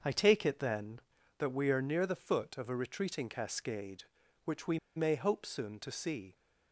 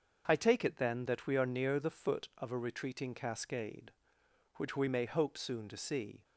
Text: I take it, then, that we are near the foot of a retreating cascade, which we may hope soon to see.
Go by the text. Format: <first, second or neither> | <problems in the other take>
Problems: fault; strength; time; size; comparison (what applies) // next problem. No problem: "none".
second | starts louder than the rest; until 1.4 s; 6.5 dB; also in the second // pauses between "we" and "may"; slight; at 4.7 s; 0.18 s long